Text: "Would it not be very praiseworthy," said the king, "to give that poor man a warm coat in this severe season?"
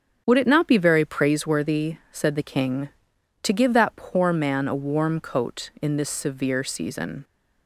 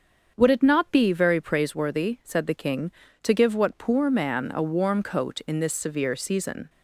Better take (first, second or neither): first